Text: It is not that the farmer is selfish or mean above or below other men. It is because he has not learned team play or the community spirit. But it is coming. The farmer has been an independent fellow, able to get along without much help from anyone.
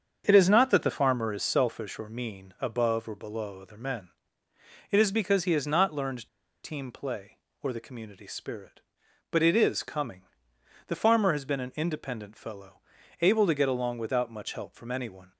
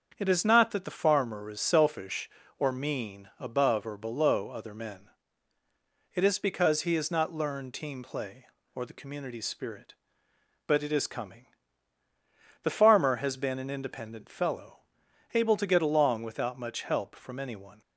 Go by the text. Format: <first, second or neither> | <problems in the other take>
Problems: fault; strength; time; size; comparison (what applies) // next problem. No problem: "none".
second | starts louder than the rest; until 1.2 s; 7 dB; strong in the second // pauses between "learned" and "team"; slight; at 6.2 s; 0.36 s long